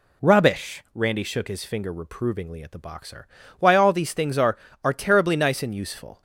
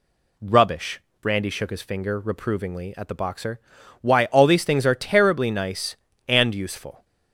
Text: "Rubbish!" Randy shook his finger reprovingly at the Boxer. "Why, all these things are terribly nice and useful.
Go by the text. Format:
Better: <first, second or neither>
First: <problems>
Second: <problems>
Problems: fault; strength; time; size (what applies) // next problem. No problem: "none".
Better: second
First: says "are" twice; at 4.8 s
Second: none